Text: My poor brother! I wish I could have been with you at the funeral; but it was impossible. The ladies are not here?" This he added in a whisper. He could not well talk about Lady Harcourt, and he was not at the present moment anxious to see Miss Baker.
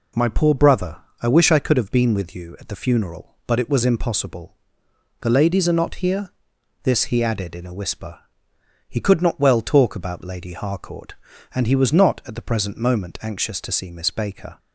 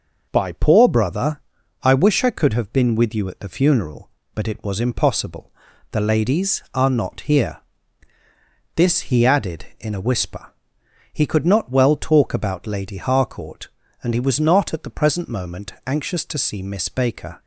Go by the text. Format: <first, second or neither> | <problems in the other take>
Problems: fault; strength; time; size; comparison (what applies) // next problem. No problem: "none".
first | says "By" for "My"; at 0.2 s